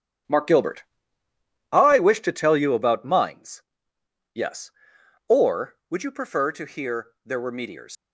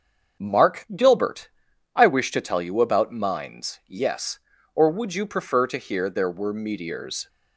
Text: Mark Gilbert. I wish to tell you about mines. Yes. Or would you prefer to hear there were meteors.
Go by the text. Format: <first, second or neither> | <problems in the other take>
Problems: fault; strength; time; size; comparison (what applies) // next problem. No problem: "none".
second | starts louder than the rest; strong; until 2.1 s; 10 dB; also in the second // pauses between "hear" and "there"; slight; at 7.0 s; 0.16 s long // leaves "meteors" unfinished; at 7.9 s; 100 ms